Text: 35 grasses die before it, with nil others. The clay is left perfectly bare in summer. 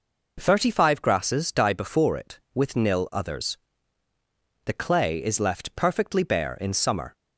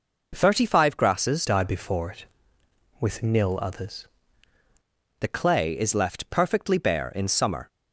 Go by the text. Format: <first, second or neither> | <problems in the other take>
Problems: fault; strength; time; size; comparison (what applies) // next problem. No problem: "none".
first | changes voice from "die" to "others"; from 1.4 to 4.0 s; 2.6 s long